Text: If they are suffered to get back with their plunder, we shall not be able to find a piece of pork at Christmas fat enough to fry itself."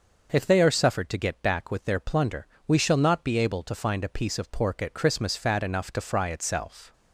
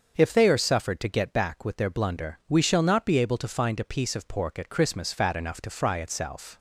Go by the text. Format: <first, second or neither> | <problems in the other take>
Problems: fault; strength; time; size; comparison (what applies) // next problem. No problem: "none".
first | starts louder than the rest; until 1.1 s; 6.5 dB; noticeable in the first // says "blunder" for "plunder"; at 1.8 s